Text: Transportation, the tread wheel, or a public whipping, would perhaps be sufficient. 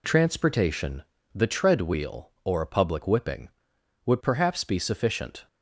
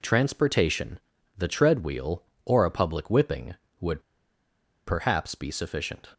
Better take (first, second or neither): first